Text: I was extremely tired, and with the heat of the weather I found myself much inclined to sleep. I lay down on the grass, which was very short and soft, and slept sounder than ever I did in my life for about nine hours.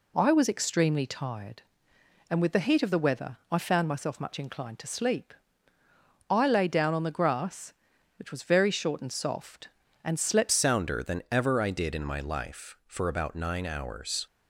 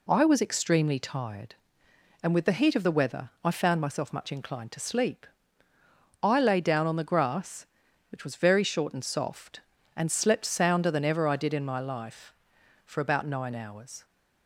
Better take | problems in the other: second | changes voice at "sounder"; from 10.5 s on; 3.7 s long

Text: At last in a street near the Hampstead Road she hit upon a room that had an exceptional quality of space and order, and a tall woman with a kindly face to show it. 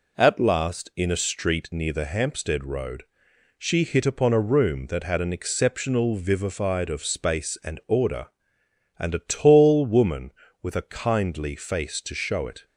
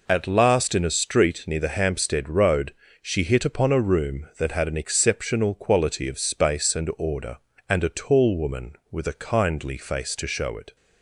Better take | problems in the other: second | pauses between "Road" and "she"; noticeable; at 3.0 s; 0.56 s long; slight in the second // says "vivified" for "quality"; at 6.1 s

